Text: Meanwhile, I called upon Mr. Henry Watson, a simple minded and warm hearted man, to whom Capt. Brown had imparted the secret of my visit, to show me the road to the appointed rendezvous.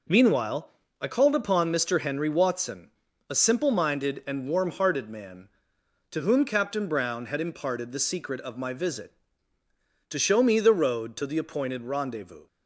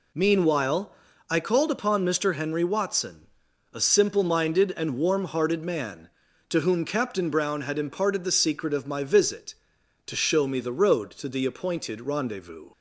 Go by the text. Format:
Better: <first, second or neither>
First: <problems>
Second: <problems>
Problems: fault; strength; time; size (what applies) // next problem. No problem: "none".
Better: neither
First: none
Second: none